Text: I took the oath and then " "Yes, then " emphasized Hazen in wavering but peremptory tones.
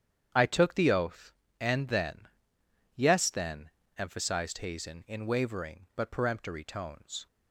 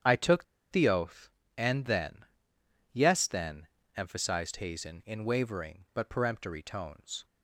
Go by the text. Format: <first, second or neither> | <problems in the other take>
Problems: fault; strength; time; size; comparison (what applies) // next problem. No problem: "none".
first | starts louder than the rest; strong; until 1.5 s; 8 dB; strong in the first // pauses between "took" and "the"; slight; at 0.4 s; 0.28 s long